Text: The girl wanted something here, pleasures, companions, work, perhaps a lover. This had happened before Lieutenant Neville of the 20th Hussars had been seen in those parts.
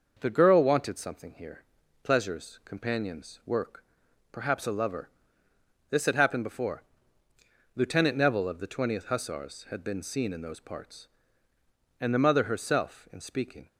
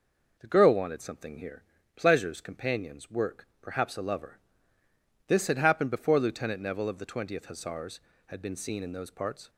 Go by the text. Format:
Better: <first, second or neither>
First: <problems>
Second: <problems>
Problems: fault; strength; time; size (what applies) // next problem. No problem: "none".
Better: second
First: starts louder than the rest; noticeable; until 1.2 s; 6 dB // pauses between "before" and "Lieutenant"; noticeable; at 6.8 s; 0.94 s long // goes on to say "And the mother herself in speaking"; strong; from 11.9 s on; 1.6 s long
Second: none